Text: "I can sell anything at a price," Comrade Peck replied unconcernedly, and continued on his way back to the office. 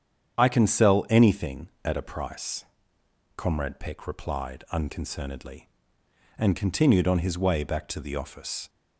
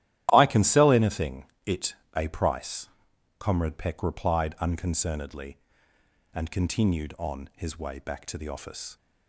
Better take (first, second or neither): first